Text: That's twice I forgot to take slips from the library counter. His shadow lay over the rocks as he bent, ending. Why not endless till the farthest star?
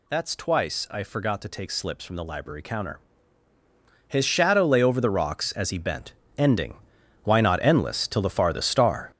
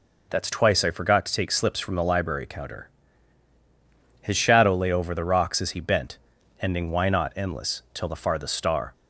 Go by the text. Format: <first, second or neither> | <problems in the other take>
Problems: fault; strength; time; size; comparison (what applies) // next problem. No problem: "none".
second | gets louder; strong; throughout; 8.5 dB